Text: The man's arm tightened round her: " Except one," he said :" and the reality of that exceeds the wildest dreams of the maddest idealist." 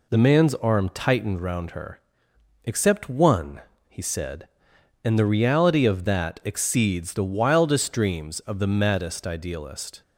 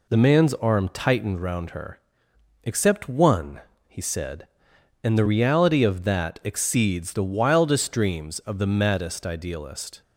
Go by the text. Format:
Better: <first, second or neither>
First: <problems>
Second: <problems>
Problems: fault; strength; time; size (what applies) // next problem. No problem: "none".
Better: neither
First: none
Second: none